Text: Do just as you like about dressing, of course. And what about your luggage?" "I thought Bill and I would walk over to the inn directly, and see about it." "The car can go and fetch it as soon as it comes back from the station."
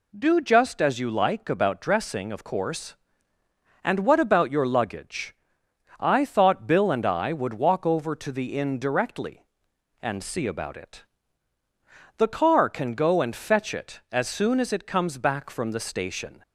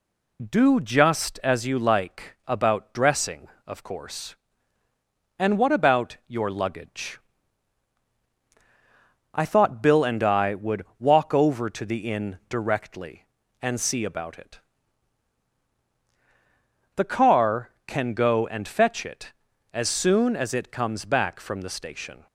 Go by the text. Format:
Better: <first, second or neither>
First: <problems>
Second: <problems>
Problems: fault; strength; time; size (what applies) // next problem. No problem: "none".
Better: first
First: none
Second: loses the start of "Do"; at 0.3 s; 45 ms